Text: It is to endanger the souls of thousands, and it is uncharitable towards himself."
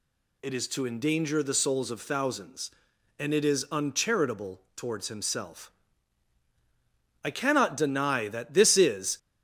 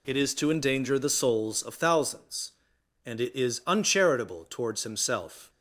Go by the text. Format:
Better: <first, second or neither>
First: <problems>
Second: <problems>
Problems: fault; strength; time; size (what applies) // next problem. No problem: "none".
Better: second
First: goes on to say "I cannot deny that this is"; strong; from 7.2 s on; 1.9 s long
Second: none